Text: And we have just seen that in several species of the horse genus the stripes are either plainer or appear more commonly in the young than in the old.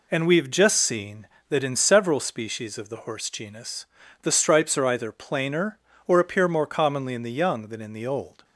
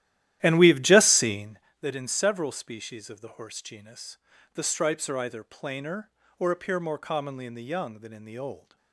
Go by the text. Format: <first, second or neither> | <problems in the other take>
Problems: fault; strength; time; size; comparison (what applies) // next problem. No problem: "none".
first | starts louder than the rest; strong; until 1.7 s; 13 dB // pauses between "genus" and "the"; slight; at 4.1 s; 0.36 s long; slight in the first